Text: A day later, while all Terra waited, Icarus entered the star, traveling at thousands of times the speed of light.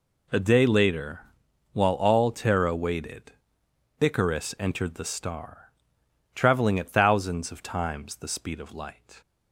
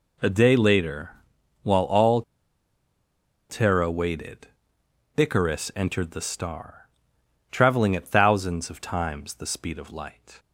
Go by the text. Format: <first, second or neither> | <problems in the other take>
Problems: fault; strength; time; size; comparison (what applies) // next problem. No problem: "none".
first | pauses between "all" and "Terra"; strong; at 2.2 s; 1.2 s long